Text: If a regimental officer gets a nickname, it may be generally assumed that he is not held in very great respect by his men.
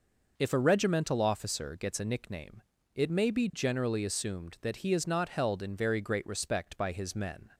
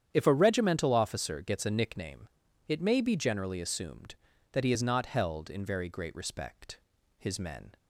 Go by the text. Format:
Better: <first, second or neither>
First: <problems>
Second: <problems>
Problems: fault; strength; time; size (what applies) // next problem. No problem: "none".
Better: first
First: none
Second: starts louder than the rest; strong; until 1.1 s; 9 dB // skips "by"; at 6.9 s